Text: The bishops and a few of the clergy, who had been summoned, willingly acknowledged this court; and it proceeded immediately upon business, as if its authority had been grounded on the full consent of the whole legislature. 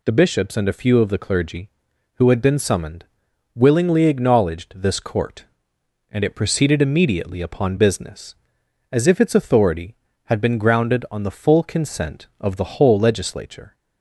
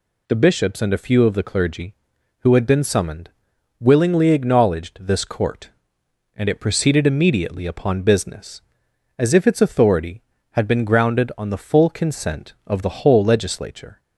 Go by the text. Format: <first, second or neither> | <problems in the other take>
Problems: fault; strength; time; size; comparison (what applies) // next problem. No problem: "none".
neither | none